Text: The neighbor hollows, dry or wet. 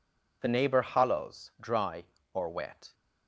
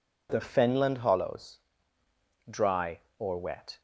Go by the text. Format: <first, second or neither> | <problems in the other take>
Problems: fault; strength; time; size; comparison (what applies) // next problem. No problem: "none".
first | says "fenland" for "neighbor"; at 0.3 s